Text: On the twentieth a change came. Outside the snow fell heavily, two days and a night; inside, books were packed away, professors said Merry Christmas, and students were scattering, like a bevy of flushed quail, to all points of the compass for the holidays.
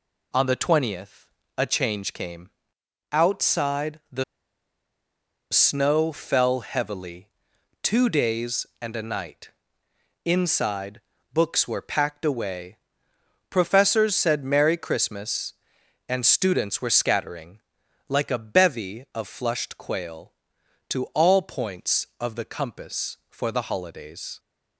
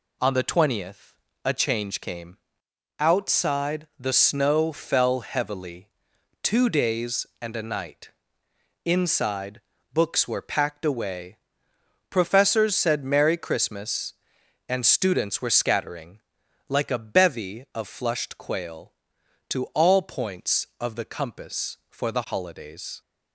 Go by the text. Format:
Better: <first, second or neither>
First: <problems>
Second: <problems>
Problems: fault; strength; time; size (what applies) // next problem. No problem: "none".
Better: second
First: pauses between "twentieth" and "a"; slight; at 1.2 s; 0.32 s long // pauses between "the" and "snow"; strong; at 4.2 s; 1.2 s long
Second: pauses between "twentieth" and "a"; slight; at 1.1 s; 0.32 s long